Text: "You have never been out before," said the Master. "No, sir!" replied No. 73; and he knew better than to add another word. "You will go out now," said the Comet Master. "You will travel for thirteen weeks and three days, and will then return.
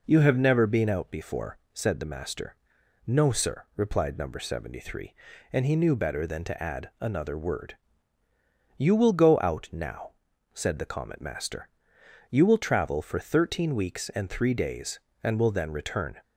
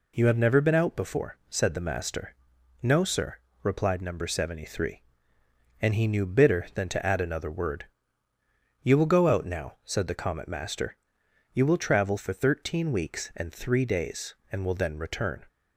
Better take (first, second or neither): first